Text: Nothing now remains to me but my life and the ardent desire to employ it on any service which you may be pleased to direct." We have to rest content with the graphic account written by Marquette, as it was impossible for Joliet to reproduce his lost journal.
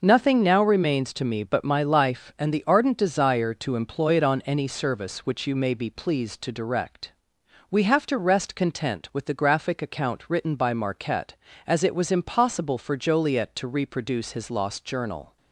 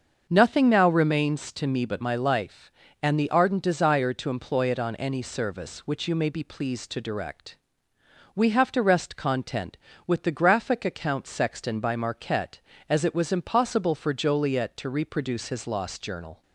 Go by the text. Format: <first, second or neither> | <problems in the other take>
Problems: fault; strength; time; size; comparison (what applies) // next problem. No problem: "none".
first | starts louder than the rest; until 1.3 s; 6.5 dB // says "sexton" for "written"; at 11.2 s